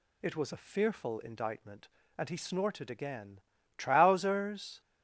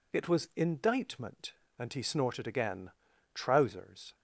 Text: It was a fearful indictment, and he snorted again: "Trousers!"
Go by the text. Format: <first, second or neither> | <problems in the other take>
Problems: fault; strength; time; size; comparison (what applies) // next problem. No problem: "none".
first | skips "a fearful"; at 0.5 s